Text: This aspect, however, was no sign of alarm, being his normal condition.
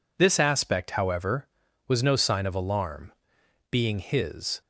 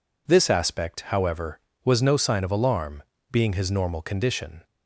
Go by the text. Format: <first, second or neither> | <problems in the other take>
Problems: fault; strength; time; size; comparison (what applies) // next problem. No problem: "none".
second | stops before "normal condition"; at 4.6 s